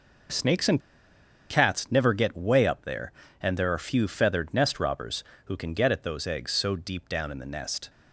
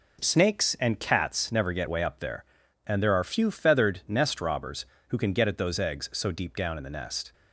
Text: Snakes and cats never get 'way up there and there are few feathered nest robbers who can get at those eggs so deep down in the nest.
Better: second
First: pauses between "and" and "cats"; noticeable; at 0.7 s; 0.71 s long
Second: none

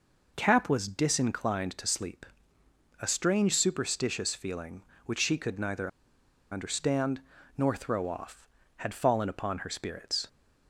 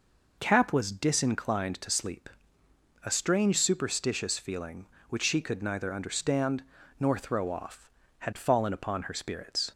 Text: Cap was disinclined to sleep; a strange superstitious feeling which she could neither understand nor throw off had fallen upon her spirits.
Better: second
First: pauses between "neither" and "understand"; noticeable; at 5.8 s; 0.63 s long // pauses between "understand" and "nor"; at 7.1 s; 0.38 s long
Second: pauses between "understand" and "nor"; at 6.6 s; 0.38 s long

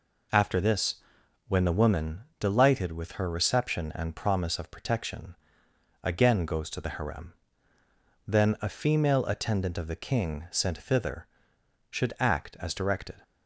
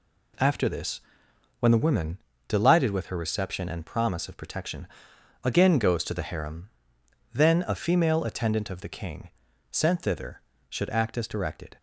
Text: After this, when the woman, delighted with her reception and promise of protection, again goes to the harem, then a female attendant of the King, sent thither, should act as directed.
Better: neither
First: none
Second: none

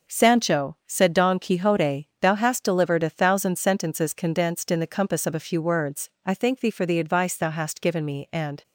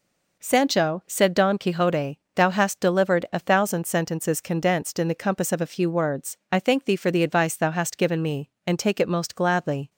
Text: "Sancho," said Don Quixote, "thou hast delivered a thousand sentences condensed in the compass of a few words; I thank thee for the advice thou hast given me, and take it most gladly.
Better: second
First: starts louder than the rest; noticeable; until 1.1 s; 6 dB // stops before "take it most gladly"; at 8.6 s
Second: none

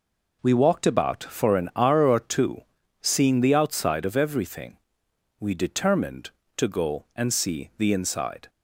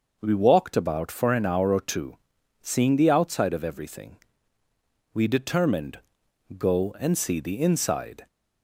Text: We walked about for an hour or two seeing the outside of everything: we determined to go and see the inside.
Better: first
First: pauses between "two" and "seeing"; at 2.6 s; 0.40 s long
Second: pauses between "two" and "seeing"; at 2.1 s; 0.44 s long // skips "to"; at 6.2 s

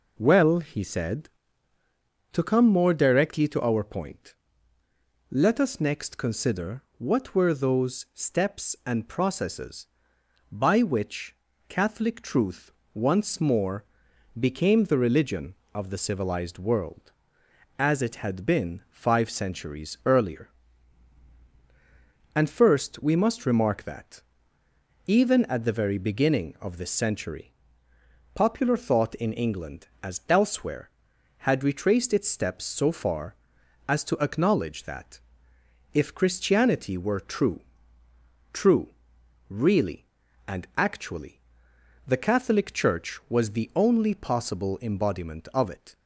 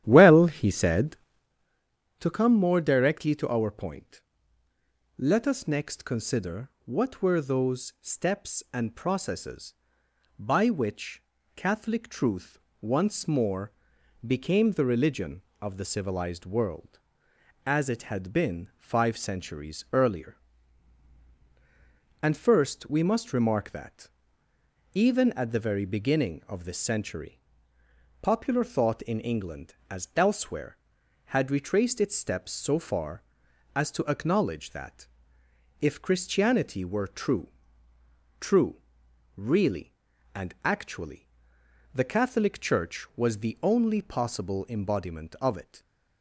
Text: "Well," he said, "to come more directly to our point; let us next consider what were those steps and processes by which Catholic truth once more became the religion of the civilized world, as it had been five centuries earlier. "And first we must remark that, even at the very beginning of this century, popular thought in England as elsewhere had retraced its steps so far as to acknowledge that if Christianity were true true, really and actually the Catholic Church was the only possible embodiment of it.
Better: first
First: pauses between "consider" and "what"; slight; at 6.8 s; 0.16 s long // pauses between "which" and "Catholic"; slight; at 11.3 s; 0.34 s long // pauses between "truth" and "once"; slight; at 12.7 s; 0.22 s long // pauses between "more" and "became"; noticeable; at 13.8 s; 0.54 s long // pauses between "that" and "if"; noticeable; at 35.2 s; 0.72 s long // pauses between "true" and "true"; noticeable; at 37.6 s; 0.92 s long // pauses between "actually" and "the"; noticeable; at 41.4 s; 0.66 s long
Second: starts louder than the rest; strong; until 1.5 s; 11.5 dB // pauses between "consider" and "what"; slight; at 6.6 s; 0.16 s long // pauses between "which" and "Catholic"; slight; at 11.2 s; 0.34 s long // pauses between "truth" and "once"; slight; at 12.5 s; 0.22 s long // pauses between "more" and "became"; noticeable; at 13.7 s; 0.54 s long // pauses between "that" and "if"; noticeable; at 35.0 s; 0.72 s long // pauses between "true" and "true"; noticeable; at 37.4 s; 0.92 s long // pauses between "actually" and "the"; noticeable; at 41.2 s; 0.66 s long

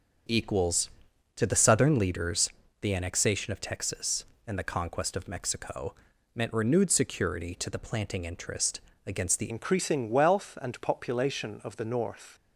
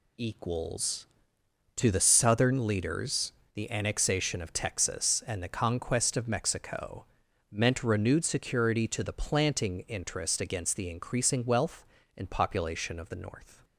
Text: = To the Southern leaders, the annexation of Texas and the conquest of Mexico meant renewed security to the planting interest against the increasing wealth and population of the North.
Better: second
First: starts louder than the rest; until 1.7 s; 6.5 dB // pauses between "Mexico" and "meant"; at 5.9 s; 0.40 s long // pauses between "interest" and "against"; slight; at 8.8 s; 0.24 s long // changes voice at "increasing"; from 9.4 s on; 2.9 s long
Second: pauses between "Mexico" and "meant"; noticeable; at 7.0 s; 0.46 s long

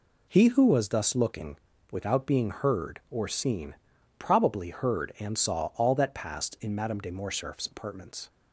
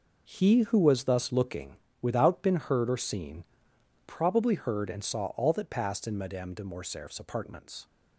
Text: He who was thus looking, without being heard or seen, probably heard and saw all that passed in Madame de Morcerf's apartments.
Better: first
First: none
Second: says "been" for "being"; at 2.4 s

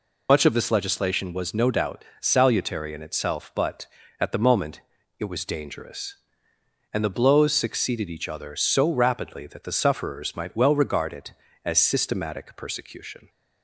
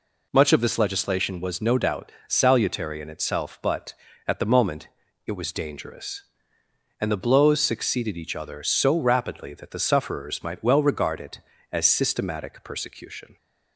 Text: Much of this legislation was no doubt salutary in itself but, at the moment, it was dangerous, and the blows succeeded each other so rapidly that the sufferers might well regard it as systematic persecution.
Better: second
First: loses the start of "Much"; at 0.2 s; 65 ms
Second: none

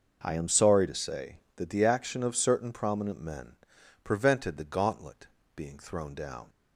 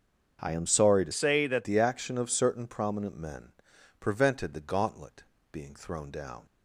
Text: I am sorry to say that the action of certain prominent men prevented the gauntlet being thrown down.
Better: first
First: pauses between "men" and "prevented"; noticeable; at 3.5 s; 0.48 s long // pauses between "gauntlet" and "being"; slight; at 5.2 s; 0.28 s long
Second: starts louder than the rest; until 1.4 s; 7 dB // changes voice from "say" to "that"; from 1.1 to 1.6 s; 0.5 s long // pauses between "men" and "prevented"; noticeable; at 3.5 s; 0.48 s long // pauses between "gauntlet" and "being"; slight; at 5.2 s; 0.28 s long

